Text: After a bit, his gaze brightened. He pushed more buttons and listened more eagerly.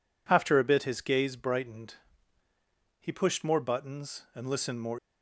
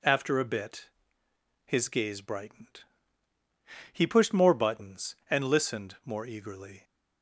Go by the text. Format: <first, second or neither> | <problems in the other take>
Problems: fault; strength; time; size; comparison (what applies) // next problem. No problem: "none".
second | stops before "eagerly"; at 4.9 s